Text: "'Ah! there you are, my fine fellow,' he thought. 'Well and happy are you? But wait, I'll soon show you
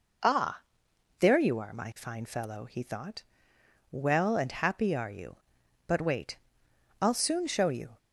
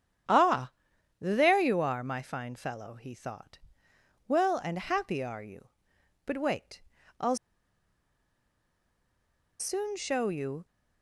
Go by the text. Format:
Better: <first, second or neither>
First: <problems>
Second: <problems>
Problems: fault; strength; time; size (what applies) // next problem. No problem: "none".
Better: first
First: none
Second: starts louder than the rest; strong; until 1.7 s; 9 dB // pauses between "I'll" and "soon"; strong; at 7.3 s; 2.2 s long